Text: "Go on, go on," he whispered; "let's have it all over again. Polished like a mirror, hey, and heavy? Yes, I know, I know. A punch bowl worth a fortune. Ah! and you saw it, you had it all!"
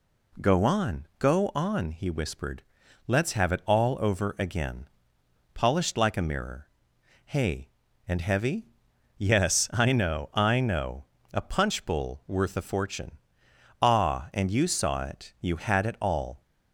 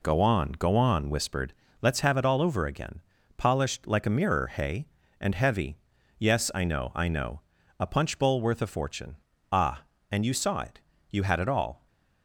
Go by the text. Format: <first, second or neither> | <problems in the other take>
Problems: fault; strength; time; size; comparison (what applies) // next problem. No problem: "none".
first | skips "he"; at 1.1 s